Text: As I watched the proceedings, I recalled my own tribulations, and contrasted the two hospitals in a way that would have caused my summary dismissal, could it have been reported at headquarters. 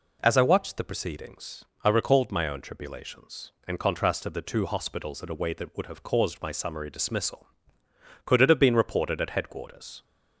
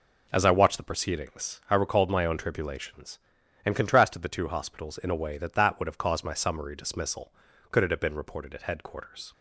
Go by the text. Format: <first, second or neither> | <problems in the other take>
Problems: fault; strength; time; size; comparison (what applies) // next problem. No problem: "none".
first | says "that" twice; at 5.5 s